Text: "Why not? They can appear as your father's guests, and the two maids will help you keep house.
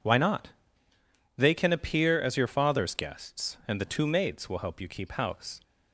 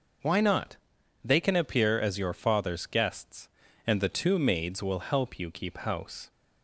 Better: neither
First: none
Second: none

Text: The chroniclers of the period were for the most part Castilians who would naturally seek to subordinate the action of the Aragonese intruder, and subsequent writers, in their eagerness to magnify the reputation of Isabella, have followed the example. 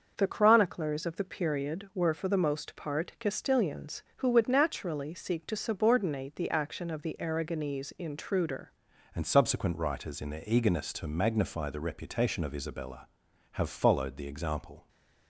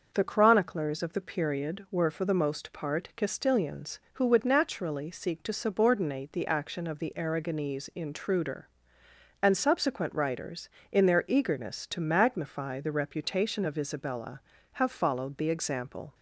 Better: second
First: starts louder than the rest; until 1.1 s; 6 dB // changes voice at "and"; from 9.1 s on; 5.7 s long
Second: starts louder than the rest; until 1.1 s; 6 dB

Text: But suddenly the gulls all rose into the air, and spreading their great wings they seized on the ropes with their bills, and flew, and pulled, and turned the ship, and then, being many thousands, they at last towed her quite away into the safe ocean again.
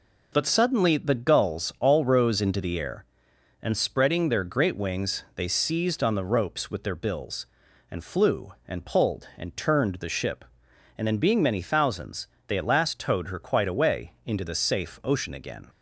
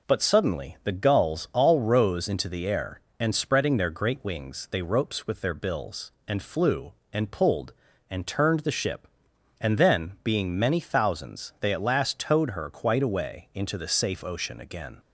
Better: first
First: none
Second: skips "seized on the"; at 4.8 s

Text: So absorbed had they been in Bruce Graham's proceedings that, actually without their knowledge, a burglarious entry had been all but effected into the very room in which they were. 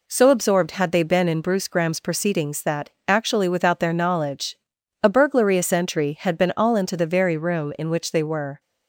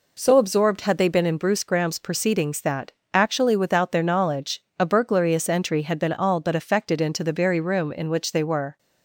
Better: second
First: skips "but effected"; at 6.7 s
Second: none

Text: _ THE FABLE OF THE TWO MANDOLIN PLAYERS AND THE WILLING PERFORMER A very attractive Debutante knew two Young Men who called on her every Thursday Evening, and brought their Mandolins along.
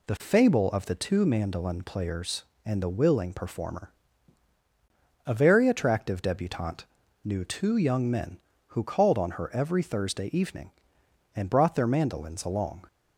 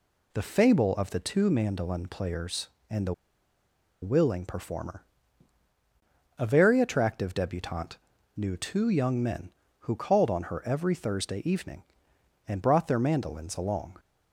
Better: first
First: pauses between "PERFORMER" and "A"; strong; at 3.8 s; 1.3 s long // pauses between "Debutante" and "knew"; at 6.8 s; 0.38 s long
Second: pauses between "THE" and "WILLING"; noticeable; at 3.1 s; 0.89 s long // pauses between "PERFORMER" and "A"; strong; at 5.0 s; 1.3 s long // pauses between "Debutante" and "knew"; at 7.9 s; 0.38 s long

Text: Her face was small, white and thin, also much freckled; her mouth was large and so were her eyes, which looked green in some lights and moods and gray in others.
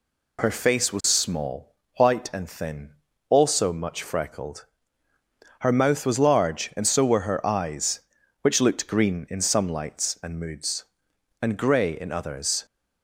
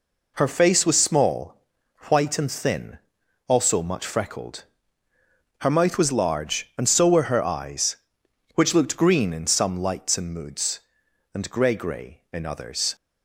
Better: first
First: none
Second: says "gray" twice; at 11.7 s

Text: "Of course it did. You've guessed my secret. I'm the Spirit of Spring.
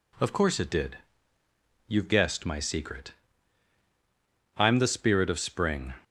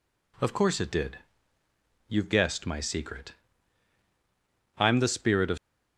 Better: first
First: none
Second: stops before "Spring"; at 5.5 s

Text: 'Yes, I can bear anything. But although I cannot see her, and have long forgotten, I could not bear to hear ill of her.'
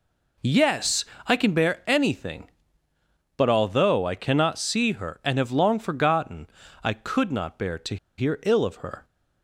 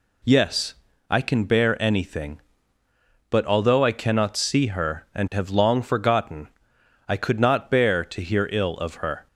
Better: second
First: pauses between "to" and "hear"; slight; at 7.9 s; 0.22 s long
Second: none

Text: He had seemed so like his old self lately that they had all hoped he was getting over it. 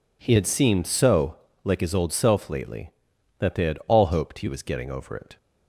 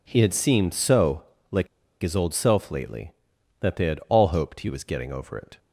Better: first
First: pauses between "so" and "like"; slight; at 1.3 s; 0.28 s long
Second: pauses between "so" and "like"; slight; at 1.2 s; 0.28 s long // pauses between "like" and "his"; slight; at 1.6 s; 0.34 s long

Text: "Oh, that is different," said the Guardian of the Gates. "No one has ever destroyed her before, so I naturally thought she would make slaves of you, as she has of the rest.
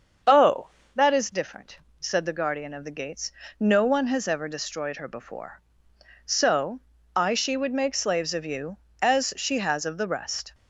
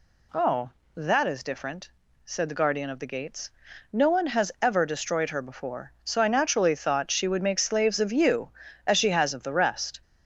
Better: second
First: starts louder than the rest; until 1.5 s; 7 dB // pauses between "so" and "I"; slight; at 6.8 s; 0.34 s long // skips "naturally thought"; at 7.3 s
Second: none

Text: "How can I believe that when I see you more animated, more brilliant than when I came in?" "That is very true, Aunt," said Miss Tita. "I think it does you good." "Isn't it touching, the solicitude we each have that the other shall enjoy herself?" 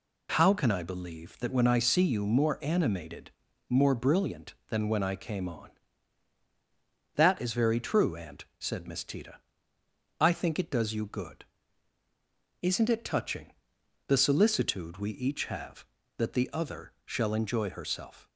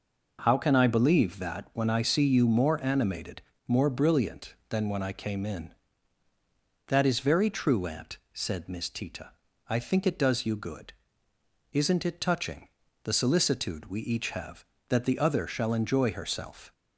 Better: second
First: says "on" for "in"; at 5.4 s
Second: none

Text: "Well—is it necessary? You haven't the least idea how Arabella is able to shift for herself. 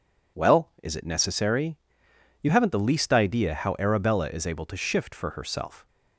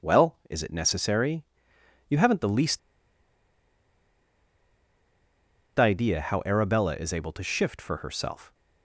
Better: first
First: none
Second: pauses between "least" and "idea"; strong; at 2.7 s; 3.0 s long

